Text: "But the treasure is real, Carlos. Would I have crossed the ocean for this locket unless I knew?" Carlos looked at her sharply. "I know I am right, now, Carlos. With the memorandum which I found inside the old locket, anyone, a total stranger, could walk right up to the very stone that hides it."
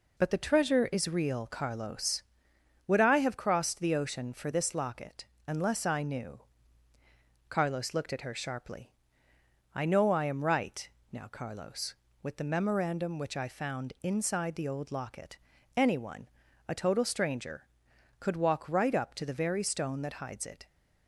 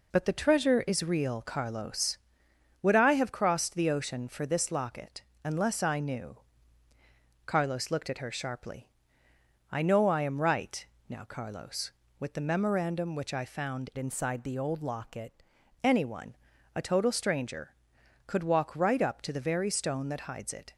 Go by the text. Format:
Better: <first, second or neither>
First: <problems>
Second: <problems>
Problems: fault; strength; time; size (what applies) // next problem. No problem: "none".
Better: first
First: pauses between "locket" and "unless"; slight; at 5.2 s; 0.22 s long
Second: pauses between "locket" and "unless"; slight; at 5.2 s; 0.22 s long // changes voice from "inside" to "locket"; from 13.9 to 15.4 s; 1.5 s long